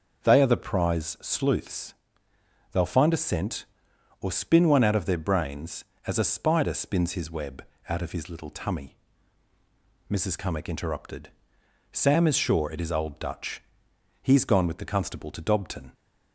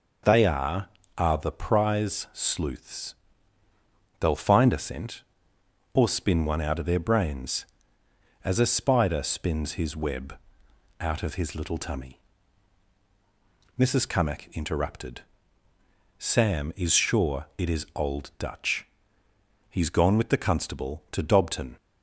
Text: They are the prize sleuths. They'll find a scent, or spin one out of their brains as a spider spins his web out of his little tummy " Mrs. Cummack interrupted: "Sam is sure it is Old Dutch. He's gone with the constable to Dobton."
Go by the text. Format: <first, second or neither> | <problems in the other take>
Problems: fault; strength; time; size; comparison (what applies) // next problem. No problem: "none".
first | says "are" twice; at 1.1 s // pauses between "web" and "out"; noticeable; at 10.3 s; 0.64 s long; slight in the first